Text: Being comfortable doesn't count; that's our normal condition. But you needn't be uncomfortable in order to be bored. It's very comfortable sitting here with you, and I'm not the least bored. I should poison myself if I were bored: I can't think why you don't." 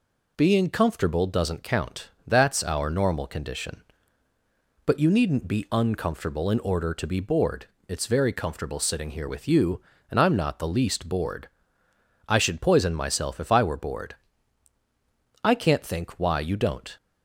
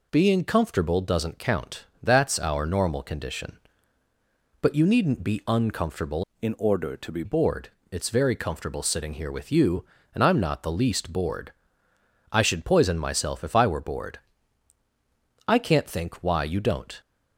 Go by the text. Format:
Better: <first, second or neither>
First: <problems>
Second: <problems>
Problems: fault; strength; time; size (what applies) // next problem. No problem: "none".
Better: first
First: none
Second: changes voice from "in" to "be"; from 6.4 to 7.2 s; 0.8 s long